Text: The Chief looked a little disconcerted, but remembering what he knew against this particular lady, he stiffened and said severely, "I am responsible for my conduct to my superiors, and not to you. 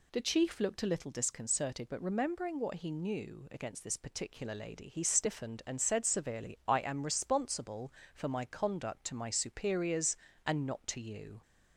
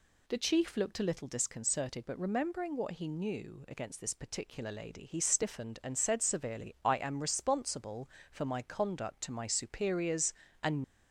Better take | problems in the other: first | stops before "not to you"; at 10.8 s

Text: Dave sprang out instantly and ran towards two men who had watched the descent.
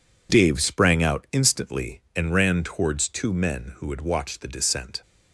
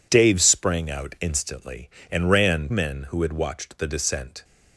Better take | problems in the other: first | skips "towards two"; at 2.7 s

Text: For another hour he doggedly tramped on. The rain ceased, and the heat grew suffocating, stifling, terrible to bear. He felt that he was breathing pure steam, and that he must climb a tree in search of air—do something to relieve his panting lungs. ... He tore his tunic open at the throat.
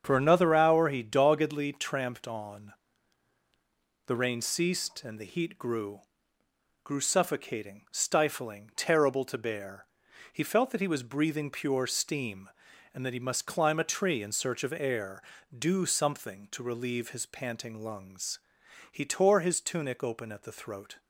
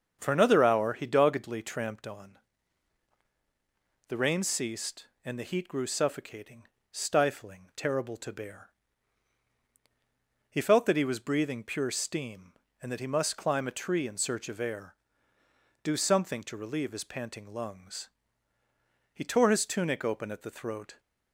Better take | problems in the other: second | starts louder than the rest; strong; until 1.0 s; 7.5 dB; also in the second // says "grew" twice; at 6.8 s

